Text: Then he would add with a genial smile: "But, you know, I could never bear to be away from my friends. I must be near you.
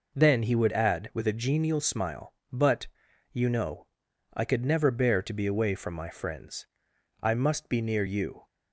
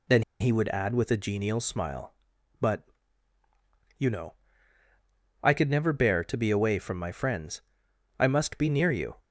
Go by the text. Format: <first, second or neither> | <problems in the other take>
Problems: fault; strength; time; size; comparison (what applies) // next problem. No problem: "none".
first | pauses between "Then" and "he"; slight; at 0.2 s; 0.17 s long